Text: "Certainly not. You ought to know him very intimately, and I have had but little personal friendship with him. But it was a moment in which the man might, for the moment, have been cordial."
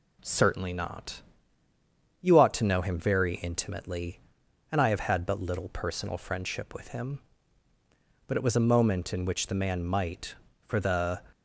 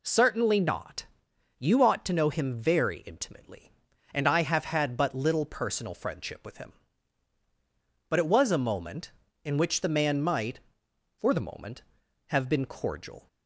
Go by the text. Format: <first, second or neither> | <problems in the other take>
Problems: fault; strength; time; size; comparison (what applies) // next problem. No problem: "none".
second | stops before "moment have been cordial"; at 11.3 s